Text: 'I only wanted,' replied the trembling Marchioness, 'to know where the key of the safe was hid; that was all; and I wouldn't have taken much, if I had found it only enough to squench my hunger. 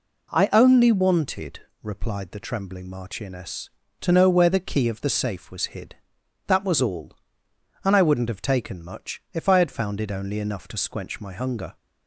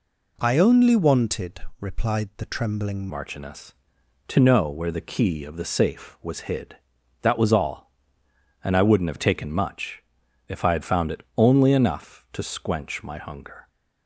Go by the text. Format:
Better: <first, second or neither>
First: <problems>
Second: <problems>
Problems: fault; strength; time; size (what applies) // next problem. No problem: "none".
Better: first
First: none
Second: changes voice at "Marchioness"; from 3.0 s on; 10.6 s long // pauses between "it" and "only"; slight; at 11.2 s; 0.16 s long